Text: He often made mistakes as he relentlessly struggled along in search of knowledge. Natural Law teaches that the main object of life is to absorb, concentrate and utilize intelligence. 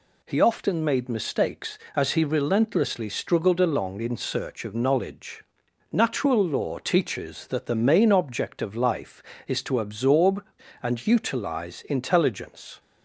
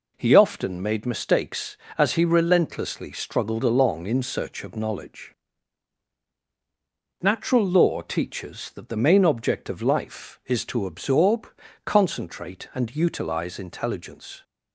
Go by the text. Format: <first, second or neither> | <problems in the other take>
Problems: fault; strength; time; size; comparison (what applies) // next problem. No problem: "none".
second | skips "concentrate"; at 10.6 s